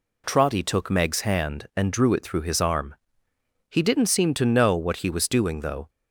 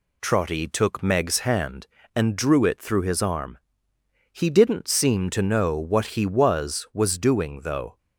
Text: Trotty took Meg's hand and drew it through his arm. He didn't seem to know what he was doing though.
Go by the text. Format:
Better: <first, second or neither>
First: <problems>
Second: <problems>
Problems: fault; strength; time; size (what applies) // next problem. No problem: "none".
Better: first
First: none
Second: says "was" twice; at 6.9 s